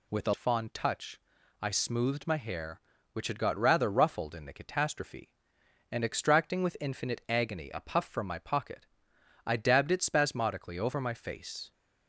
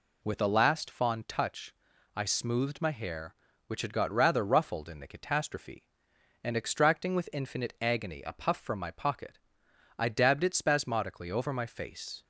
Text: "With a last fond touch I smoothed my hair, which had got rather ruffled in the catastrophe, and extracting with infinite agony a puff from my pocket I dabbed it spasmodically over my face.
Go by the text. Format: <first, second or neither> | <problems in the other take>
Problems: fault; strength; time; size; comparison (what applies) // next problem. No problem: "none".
second | skips "last"; at 0.3 s // pauses between "touch" and "I"; at 1.2 s; 0.40 s long; also in the second // pauses between "pocket" and "I"; noticeable; at 8.8 s; 0.60 s long; noticeable in the second